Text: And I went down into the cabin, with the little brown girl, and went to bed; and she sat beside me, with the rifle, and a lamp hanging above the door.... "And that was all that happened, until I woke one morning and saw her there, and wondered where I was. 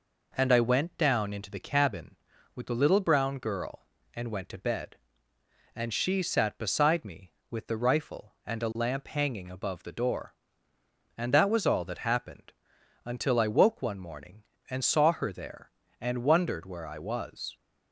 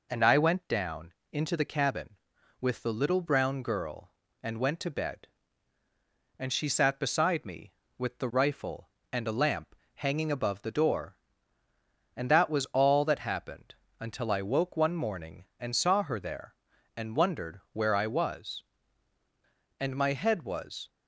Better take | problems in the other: first | pauses between "down" and "into"; slight; at 1.1 s; 0.16 s long // pauses between "lamp" and "hanging"; slight; at 9.7 s; 0.20 s long // goes on to say "And my head was"; noticeable; from 19.7 s on; 1.1 s long

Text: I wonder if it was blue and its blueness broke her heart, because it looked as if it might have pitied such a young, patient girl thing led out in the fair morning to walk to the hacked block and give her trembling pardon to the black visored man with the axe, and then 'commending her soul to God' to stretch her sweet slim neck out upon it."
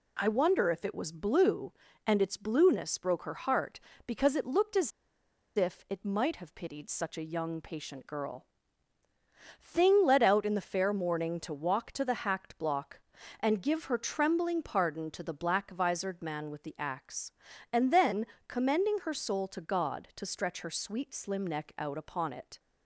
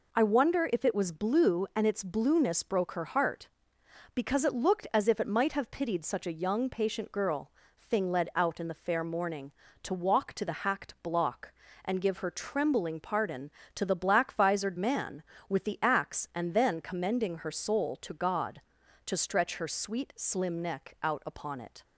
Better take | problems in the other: second | pauses between "as" and "if"; noticeable; at 4.9 s; 0.66 s long // pauses between "girl" and "thing"; at 8.4 s; 1.1 s long; slight in the second // pauses between "then" and "commending"; slight; at 18.2 s; 0.22 s long

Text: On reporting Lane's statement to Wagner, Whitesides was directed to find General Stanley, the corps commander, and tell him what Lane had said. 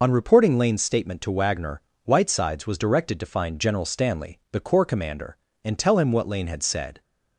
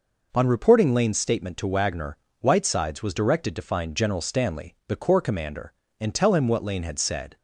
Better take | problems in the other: second | loses the start of "On"; at 0.0 s; 45 ms

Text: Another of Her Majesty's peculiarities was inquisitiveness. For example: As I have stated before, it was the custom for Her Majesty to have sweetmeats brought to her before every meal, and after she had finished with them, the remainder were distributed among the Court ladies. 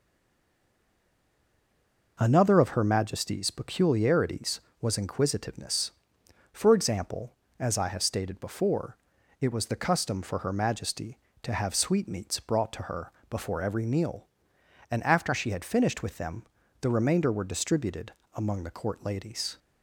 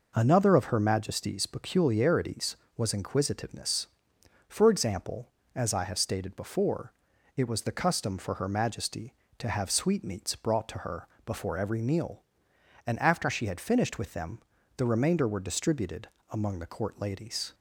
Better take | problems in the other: second | stays silent before the first word; until 2.1 s; 2.1 s long // pauses between "her" and "before"; slight; at 13.1 s; 0.18 s long; slight in the second // pauses between "distributed" and "among"; slight; at 18.1 s; 0.24 s long; slight in the second

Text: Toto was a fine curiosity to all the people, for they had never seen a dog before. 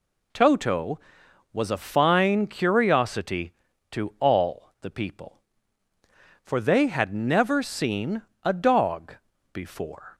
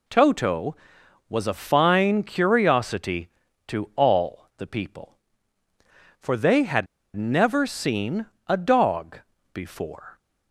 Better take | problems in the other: first | pauses between "had" and "never"; slight; at 6.8 s; 0.29 s long // pauses between "seen" and "a"; slight; at 8.2 s; 0.22 s long; slight in the first // pauses between "dog" and "before"; slight; at 9.1 s; 0.34 s long; also in the first

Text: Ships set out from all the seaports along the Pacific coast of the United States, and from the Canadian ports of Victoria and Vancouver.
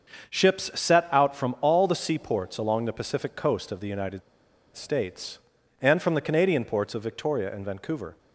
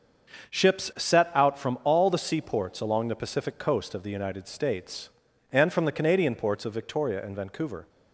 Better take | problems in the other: second | starts louder than the rest; until 1.4 s; 6.5 dB; also in the second // pauses between "United" and "States"; noticeable; at 4.2 s; 0.54 s long

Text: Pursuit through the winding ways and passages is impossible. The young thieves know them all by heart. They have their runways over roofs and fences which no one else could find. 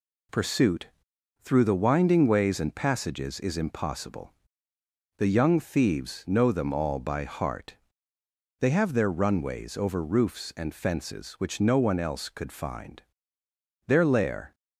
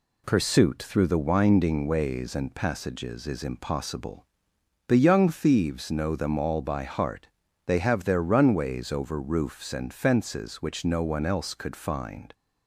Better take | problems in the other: second | pauses between "Pursuit" and "through"; noticeable; at 0.9 s; 0.52 s long // goes on to say "Their lair"; noticeable; from 13.8 s on; 0.66 s long

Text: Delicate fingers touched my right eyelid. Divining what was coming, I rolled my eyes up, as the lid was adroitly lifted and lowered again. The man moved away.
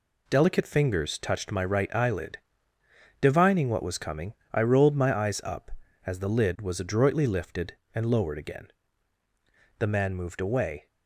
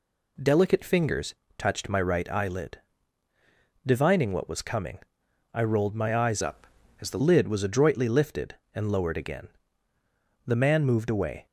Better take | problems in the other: first | pauses between "fingers" and "touched"; slight; at 1.3 s; 0.22 s long // changes voice from "up" to "the"; from 6.4 to 7.1 s; 0.7 s long

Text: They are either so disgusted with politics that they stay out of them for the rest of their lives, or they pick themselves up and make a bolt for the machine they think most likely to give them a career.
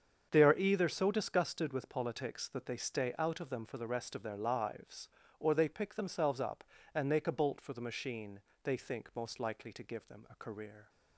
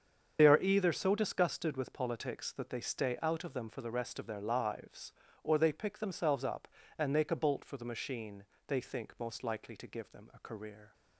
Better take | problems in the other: first | loses the start of "They"; at 0.3 s; 50 ms // starts louder than the rest; strong; until 1.4 s; 7 dB; strong in the first // pauses between "machine" and "they"; slight; at 8.4 s; 0.22 s long; slight in the first

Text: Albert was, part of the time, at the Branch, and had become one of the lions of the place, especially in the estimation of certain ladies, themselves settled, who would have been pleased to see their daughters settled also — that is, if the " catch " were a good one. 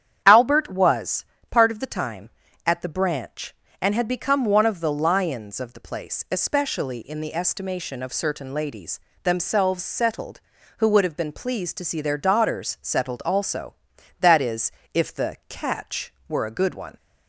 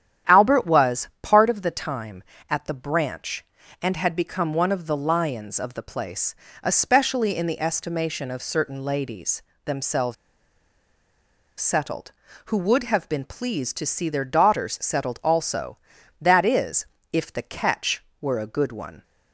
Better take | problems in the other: first | starts louder than the rest; strong; until 1.4 s; 10 dB; strong in the first // pauses between "themselves" and "settled"; strong; at 10.1 s; 1.4 s long

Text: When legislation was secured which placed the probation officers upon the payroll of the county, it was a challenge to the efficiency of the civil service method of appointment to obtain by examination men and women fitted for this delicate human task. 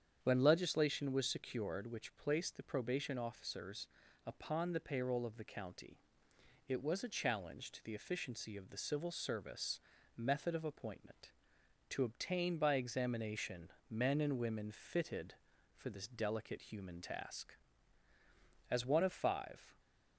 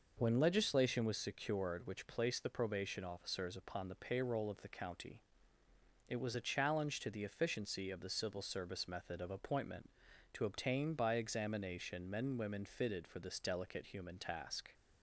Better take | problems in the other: second | starts louder than the rest; strong; until 1.2 s; 8 dB // pauses between "officers" and "upon"; at 3.8 s; 0.40 s long // pauses between "service" and "method"; at 9.7 s; 0.38 s long // pauses between "examination" and "men"; slight; at 13.6 s; 0.20 s long // goes on to say "As one of five"; noticeable; from 18.6 s on; 1.1 s long

